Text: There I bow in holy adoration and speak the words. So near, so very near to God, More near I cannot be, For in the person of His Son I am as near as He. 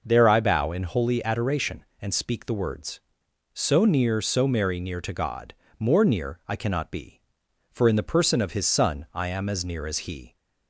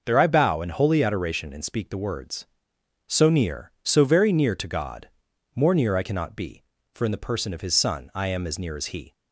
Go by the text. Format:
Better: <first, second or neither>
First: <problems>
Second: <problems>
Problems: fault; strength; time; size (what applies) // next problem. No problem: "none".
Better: second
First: says "merry" for "very"; at 4.4 s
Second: none